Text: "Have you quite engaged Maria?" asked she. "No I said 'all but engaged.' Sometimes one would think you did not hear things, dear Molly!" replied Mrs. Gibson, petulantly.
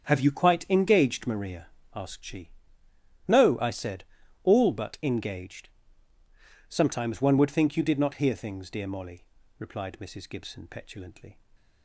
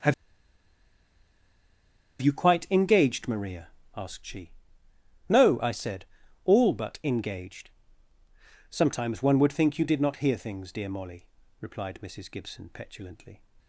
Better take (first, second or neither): first